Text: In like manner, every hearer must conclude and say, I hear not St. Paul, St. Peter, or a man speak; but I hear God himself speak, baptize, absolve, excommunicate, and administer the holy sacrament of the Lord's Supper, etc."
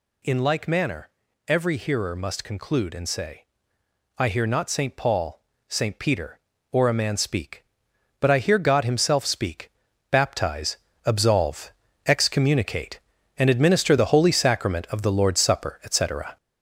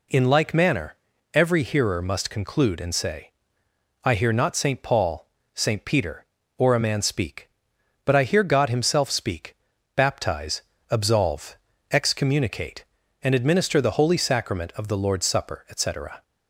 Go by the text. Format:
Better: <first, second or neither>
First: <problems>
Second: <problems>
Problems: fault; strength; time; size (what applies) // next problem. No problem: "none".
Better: second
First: gets louder; noticeable; throughout; 4.5 dB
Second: none